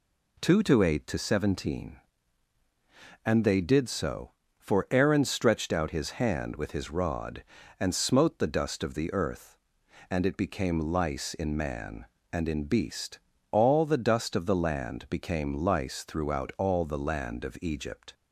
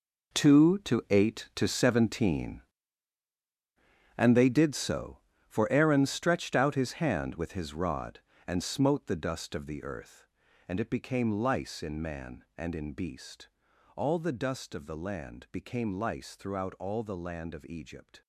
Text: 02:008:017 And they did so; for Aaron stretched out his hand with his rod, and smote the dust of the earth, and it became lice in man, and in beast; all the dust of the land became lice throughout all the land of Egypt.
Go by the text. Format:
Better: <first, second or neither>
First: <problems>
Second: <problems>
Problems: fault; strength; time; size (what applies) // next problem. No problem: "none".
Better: first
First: none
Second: gets quieter; strong; throughout; 14.5 dB